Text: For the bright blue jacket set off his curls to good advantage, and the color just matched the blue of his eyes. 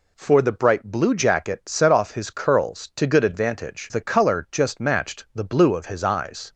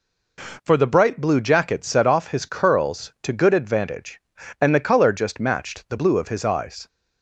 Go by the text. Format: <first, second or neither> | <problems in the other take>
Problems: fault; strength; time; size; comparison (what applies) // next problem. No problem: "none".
second | skips "and"; at 3.9 s